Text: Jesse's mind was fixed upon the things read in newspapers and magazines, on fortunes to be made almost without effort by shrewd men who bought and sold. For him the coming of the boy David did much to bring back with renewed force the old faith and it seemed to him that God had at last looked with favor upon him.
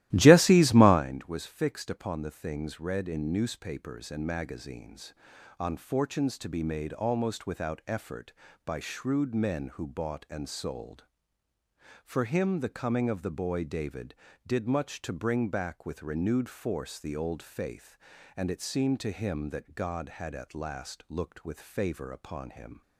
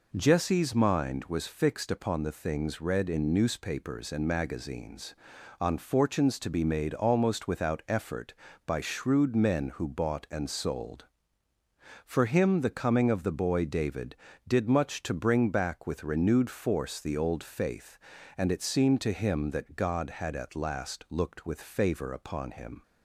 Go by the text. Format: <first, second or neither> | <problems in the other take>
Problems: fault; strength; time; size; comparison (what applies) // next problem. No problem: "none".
second | starts louder than the rest; strong; until 1.0 s; 15 dB